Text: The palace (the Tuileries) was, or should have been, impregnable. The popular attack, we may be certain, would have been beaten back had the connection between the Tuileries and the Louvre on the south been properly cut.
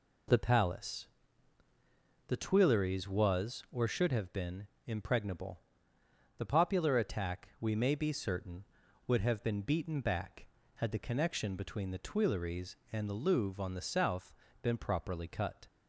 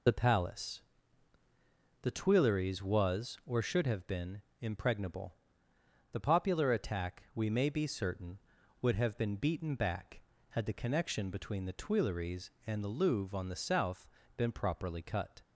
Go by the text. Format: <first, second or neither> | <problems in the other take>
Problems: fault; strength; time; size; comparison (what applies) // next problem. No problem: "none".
first | loses the start of "The"; at 0.0 s; 40 ms // pauses between "south" and "been"; slight; at 14.0 s; 0.30 s long; slight in the first